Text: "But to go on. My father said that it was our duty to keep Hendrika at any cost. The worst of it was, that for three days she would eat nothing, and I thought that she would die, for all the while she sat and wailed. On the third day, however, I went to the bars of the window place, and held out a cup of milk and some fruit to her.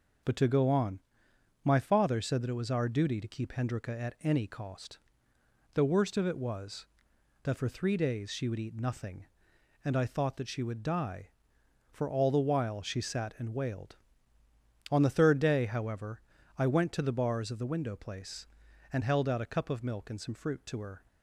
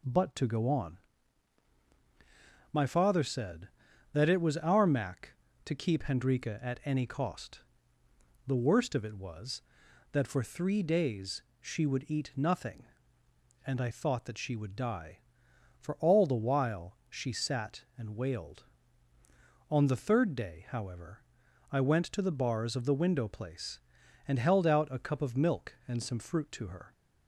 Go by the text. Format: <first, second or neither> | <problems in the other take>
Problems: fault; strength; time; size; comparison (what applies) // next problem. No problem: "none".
first | says "mac" for "duty"; at 4.8 s // pauses between "days" and "she"; slight; at 11.4 s; 0.18 s long